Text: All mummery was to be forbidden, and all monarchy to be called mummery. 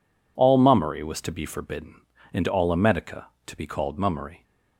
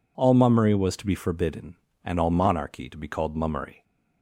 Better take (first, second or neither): second